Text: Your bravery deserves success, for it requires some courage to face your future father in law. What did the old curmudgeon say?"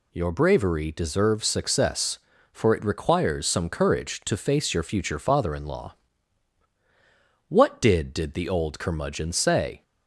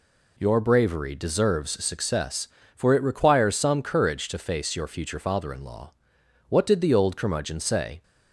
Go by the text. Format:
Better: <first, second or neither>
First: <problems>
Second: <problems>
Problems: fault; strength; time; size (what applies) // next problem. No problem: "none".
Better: second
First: says "did" twice; at 8.1 s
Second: none